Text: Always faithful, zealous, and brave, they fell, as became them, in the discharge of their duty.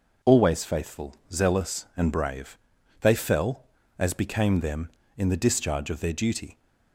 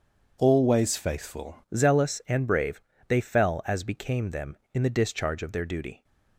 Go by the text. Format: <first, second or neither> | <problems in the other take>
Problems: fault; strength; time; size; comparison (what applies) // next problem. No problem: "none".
first | changes voice at "zealous"; from 1.7 s on; 4.3 s long